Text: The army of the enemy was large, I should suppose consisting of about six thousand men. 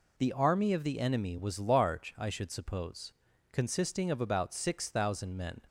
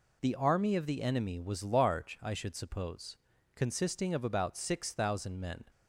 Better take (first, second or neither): neither